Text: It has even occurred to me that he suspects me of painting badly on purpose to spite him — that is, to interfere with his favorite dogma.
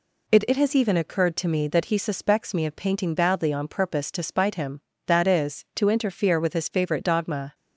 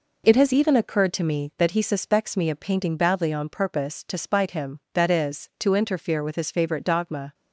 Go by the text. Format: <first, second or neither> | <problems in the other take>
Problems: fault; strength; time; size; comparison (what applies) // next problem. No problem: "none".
second | says "It" twice; at 0.4 s